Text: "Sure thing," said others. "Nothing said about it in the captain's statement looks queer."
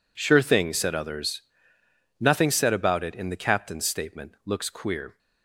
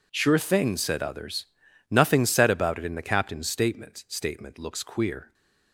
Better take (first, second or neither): first